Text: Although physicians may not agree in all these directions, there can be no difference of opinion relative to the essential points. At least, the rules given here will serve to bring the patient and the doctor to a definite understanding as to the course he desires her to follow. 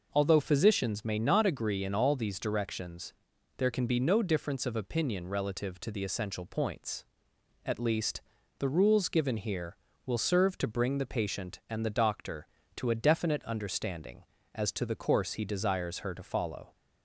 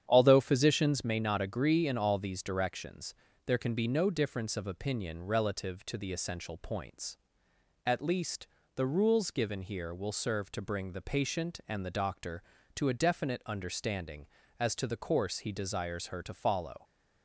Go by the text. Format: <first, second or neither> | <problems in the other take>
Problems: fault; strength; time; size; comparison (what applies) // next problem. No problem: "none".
first | starts louder than the rest; strong; until 1.1 s; 9 dB